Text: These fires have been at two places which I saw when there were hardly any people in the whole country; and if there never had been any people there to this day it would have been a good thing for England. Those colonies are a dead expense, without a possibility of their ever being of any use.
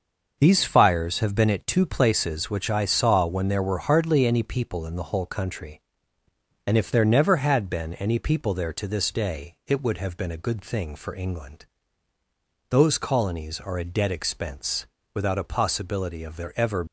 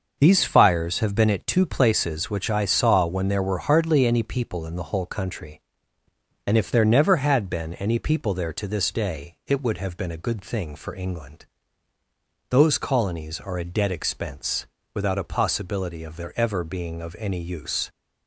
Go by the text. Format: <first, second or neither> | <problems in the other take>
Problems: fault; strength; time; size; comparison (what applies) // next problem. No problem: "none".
second | starts louder than the rest; noticeable; until 1.3 s; 6 dB; noticeable in the second // stops before "being of any use"; at 16.8 s